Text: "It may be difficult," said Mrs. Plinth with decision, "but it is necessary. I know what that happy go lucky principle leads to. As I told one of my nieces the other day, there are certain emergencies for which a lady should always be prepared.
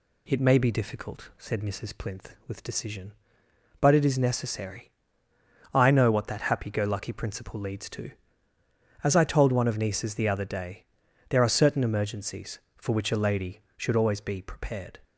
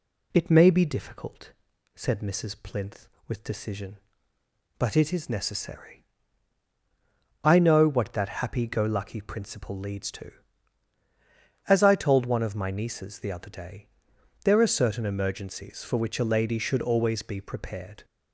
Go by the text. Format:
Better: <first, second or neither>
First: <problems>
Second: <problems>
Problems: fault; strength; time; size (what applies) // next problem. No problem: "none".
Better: second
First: skips "my"; at 9.7 s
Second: none